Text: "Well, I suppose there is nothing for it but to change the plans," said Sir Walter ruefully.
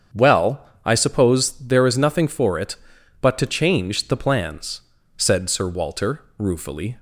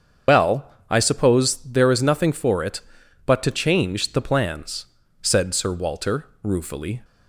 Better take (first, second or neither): first